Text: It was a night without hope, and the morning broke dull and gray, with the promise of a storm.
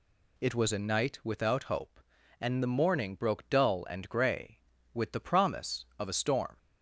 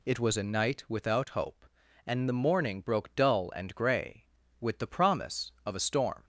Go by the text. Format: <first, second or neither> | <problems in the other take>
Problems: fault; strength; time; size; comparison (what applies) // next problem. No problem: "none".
neither | none